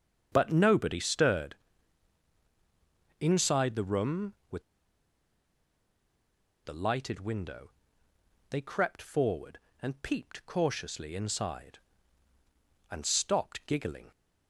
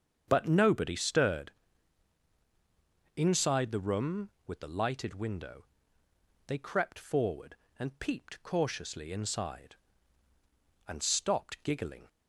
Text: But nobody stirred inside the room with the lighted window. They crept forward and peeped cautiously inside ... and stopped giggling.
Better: second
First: starts louder than the rest; strong; until 1.3 s; 7.5 dB // pauses between "stirred" and "inside"; strong; at 1.5 s; 1.6 s long // pauses between "with" and "the"; strong; at 4.6 s; 2.0 s long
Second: starts louder than the rest; strong; until 1.2 s; 7.5 dB // pauses between "stirred" and "inside"; strong; at 1.5 s; 1.6 s long

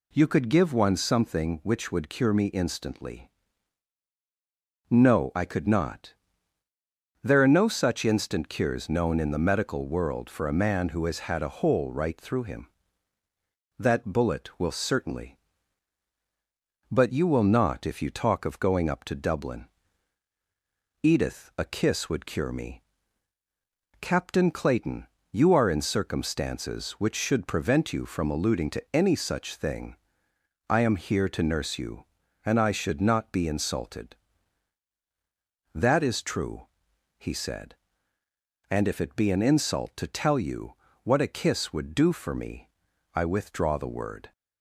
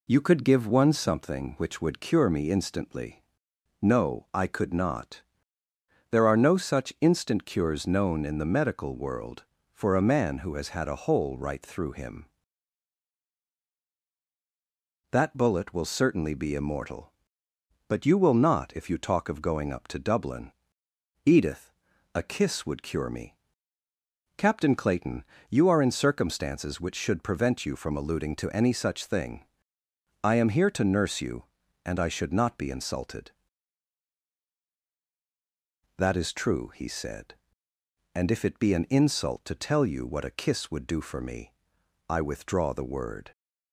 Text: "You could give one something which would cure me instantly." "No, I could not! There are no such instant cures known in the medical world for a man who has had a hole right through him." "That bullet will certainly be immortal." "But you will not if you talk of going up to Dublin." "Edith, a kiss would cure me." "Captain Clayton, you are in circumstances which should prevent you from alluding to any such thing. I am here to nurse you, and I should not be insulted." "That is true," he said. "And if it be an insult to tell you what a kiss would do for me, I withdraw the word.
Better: second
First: skips "be immortal"; at 16.1 s // pauses between "you" and "what"; slight; at 40.7 s; 0.30 s long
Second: none

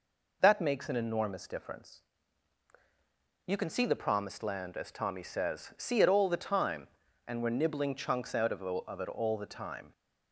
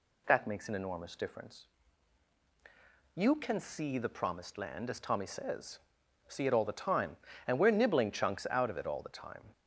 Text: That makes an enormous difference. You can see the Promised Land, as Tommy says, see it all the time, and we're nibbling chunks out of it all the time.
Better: second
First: says "of" twice; at 8.6 s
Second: none

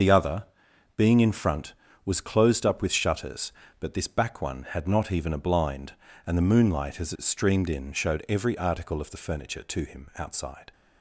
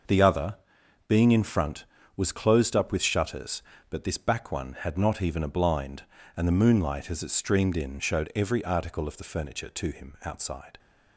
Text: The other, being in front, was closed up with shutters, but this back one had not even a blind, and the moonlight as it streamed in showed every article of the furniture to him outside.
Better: second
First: loses the start of "The"; at 0.0 s; 65 ms // starts louder than the rest; noticeable; until 1.5 s; 6 dB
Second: starts louder than the rest; noticeable; until 1.5 s; 6 dB

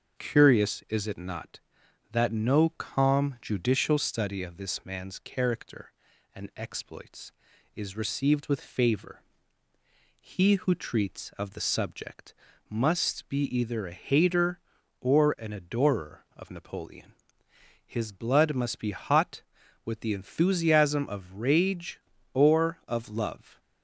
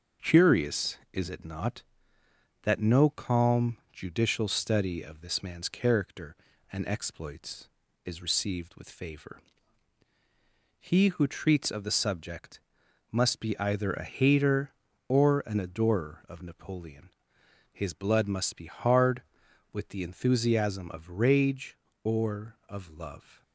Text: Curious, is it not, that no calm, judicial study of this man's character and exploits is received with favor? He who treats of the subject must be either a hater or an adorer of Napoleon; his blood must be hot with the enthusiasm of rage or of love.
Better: first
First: starts louder than the rest; until 1.2 s; 7 dB // pauses between "subject" and "must"; slight; at 12.3 s; 0.36 s long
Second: starts louder than the rest; until 1.3 s; 6.5 dB // pauses between "subject" and "must"; noticeable; at 12.5 s; 0.52 s long // says "hard" for "hot"; at 18.6 s

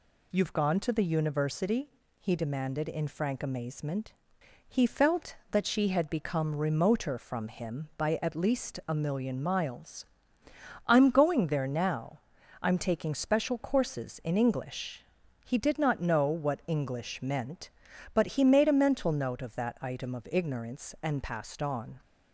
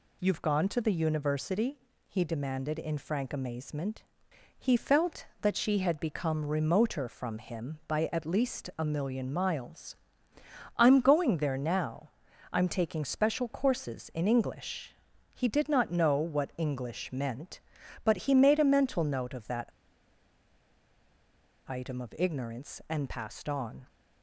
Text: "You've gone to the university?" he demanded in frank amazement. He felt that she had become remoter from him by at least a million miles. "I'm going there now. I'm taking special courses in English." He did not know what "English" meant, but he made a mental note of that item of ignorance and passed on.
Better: first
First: none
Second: pauses between "that" and "item"; strong; at 19.7 s; 1.9 s long

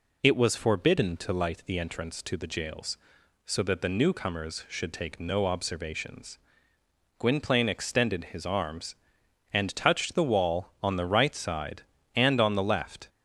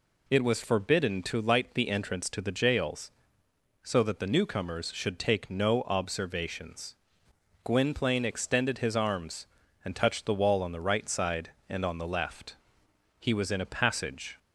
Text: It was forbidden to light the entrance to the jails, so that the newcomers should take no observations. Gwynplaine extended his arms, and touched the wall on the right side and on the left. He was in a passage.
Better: second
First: stops before "He was in a passage"; at 13.0 s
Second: none

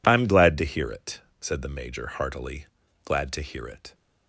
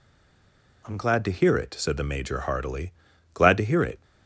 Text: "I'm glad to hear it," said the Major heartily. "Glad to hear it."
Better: first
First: none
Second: stays silent before the first word; slight; until 0.8 s; 0.8 s long

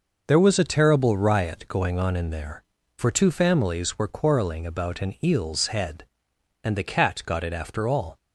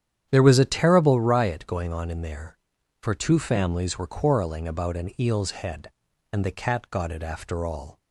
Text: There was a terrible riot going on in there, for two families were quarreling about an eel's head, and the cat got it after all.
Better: first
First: none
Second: starts louder than the rest; strong; until 1.3 s; 9.5 dB

